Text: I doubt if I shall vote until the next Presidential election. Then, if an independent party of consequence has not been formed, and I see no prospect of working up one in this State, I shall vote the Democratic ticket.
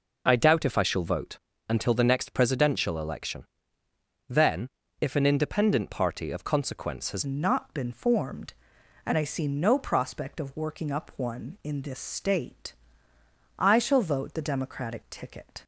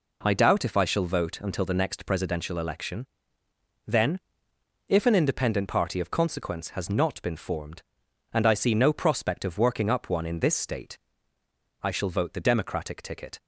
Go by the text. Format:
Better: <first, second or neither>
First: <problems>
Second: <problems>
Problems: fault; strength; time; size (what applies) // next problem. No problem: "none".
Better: second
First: pauses between "vote" and "until"; slight; at 1.3 s; 0.30 s long // changes voice at "not"; from 7.2 s on; 8.4 s long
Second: none